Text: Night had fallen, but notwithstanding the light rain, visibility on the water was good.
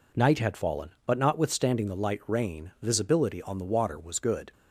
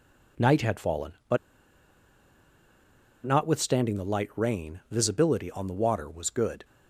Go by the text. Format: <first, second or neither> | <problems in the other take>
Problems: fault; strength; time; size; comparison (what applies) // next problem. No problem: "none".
first | pauses between "but" and "notwithstanding"; strong; at 1.3 s; 1.8 s long